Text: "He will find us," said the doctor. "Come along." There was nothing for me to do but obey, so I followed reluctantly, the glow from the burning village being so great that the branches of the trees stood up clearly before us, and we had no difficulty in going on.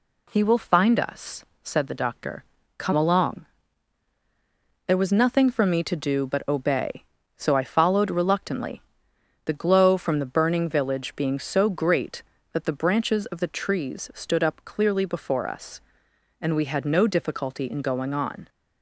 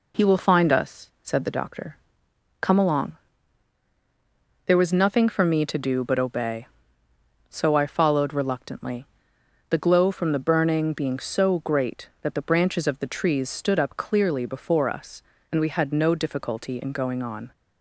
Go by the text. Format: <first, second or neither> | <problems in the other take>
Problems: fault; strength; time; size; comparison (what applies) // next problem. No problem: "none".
first | skips "village"; at 10.9 s